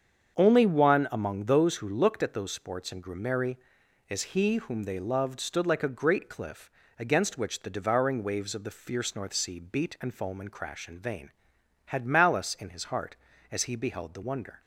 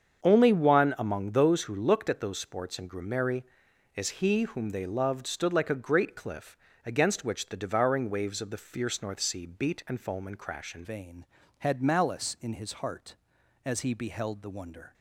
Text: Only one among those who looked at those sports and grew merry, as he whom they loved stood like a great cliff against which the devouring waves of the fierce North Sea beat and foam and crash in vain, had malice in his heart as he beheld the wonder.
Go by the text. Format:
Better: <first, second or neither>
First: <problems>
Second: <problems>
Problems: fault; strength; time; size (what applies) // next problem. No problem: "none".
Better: first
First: starts louder than the rest; strong; until 1.4 s; 7 dB // pauses between "cliff" and "against"; slight; at 6.6 s; 0.28 s long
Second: starts louder than the rest; strong; until 1.2 s; 7 dB // pauses between "cliff" and "against"; slight; at 6.5 s; 0.28 s long // changes voice at "vain"; from 10.8 s on; 4.1 s long